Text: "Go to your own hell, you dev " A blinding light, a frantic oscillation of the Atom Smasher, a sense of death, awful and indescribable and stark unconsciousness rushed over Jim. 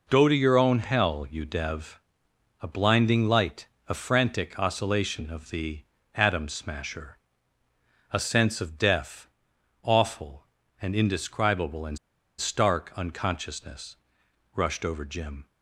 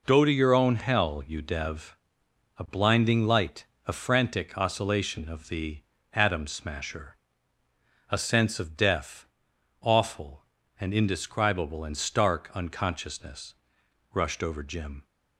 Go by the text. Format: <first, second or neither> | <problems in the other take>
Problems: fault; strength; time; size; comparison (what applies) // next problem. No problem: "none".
second | pauses between "the" and "Atom"; slight; at 5.8 s; 0.32 s long; slight in the second // pauses between "and" and "stark"; at 11.9 s; 0.41 s long // pauses between "unconsciousness" and "rushed"; noticeable; at 13.9 s; 0.58 s long; noticeable in the second